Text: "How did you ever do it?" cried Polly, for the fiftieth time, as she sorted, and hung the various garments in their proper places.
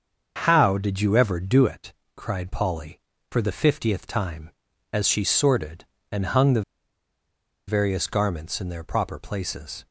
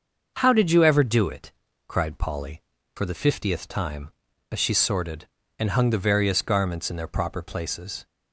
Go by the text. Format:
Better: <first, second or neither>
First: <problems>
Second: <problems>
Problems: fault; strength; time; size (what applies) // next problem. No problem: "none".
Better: second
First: starts louder than the rest; until 1.4 s; 6.5 dB // pauses between "the" and "various"; at 6.6 s; 1.0 s long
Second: starts louder than the rest; until 1.3 s; 6 dB